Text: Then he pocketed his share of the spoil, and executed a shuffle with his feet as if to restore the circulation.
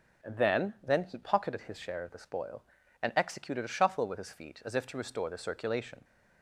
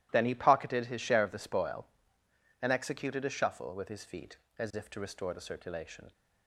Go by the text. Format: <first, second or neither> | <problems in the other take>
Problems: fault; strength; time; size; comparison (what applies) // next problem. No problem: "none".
second | says "Then" twice; at 0.8 s